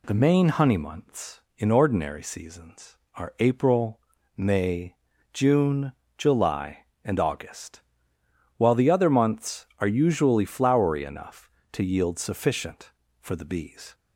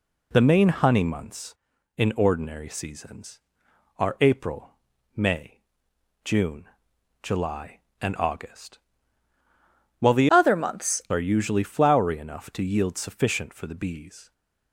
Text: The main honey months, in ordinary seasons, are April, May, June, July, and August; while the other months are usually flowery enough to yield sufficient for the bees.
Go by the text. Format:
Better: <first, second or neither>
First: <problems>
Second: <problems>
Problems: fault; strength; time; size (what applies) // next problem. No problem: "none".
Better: first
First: none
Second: changes voice from "other" to "months"; from 10.2 to 11.0 s; 0.8 s long